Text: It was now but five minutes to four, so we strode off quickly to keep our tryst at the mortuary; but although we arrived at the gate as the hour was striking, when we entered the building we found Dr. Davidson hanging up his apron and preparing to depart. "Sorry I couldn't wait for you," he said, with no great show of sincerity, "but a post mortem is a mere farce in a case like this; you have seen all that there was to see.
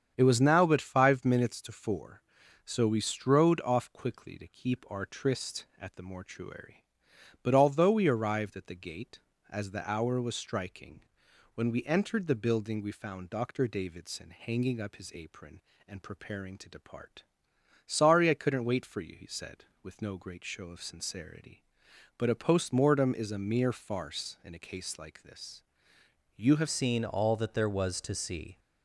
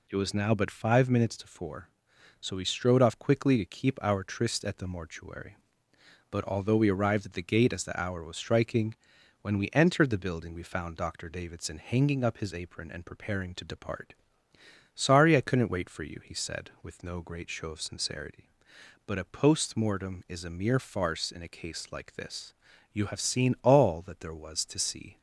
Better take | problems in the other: second | starts louder than the rest; strong; until 1.1 s; 8 dB // changes voice at "seen"; from 26.6 s on; 1.9 s long

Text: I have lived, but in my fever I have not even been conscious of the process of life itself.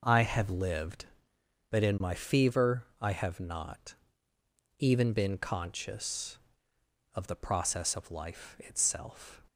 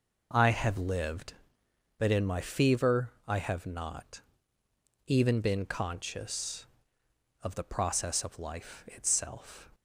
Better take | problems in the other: neither | pauses between "fever" and "I"; slight; the same in both // pauses between "not" and "even"; noticeable; the same in both

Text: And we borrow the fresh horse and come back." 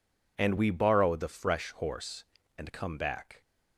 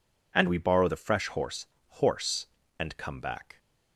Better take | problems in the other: first | says "horse" twice; at 1.8 s

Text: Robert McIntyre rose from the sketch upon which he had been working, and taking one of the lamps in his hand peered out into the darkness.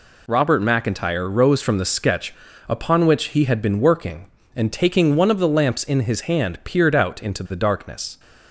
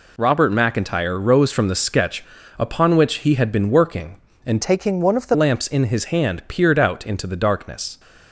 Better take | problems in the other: first | pauses between "sketch" and "upon"; slight; at 2.2 s; 0.34 s long; slight in the first // changes voice from "taking" to "the"; from 4.6 to 5.3 s; 0.7 s long

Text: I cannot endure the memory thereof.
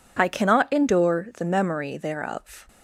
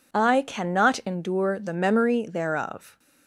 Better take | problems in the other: neither | none

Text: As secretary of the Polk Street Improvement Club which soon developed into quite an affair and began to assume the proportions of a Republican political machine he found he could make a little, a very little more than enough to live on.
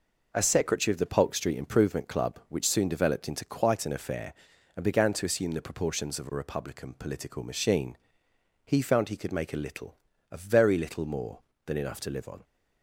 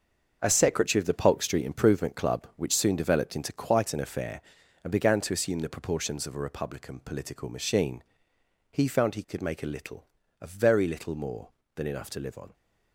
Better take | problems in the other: first | gets quieter; strong; throughout; 9.5 dB // pauses between "machine" and "he"; noticeable; at 8.0 s; 0.70 s long; noticeable in the first

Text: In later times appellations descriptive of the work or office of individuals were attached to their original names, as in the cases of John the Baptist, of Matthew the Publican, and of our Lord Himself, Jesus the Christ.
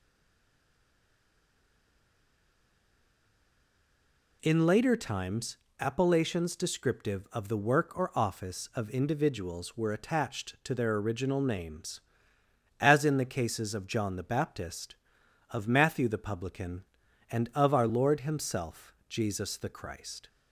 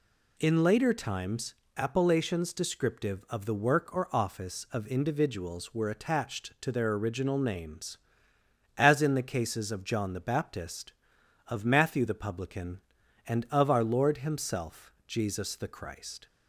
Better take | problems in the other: second | stays silent before the first word; strong; until 4.4 s; 4.4 s long // pauses between "times" and "appellations"; slight; at 5.5 s; 0.22 s long; slight in the second

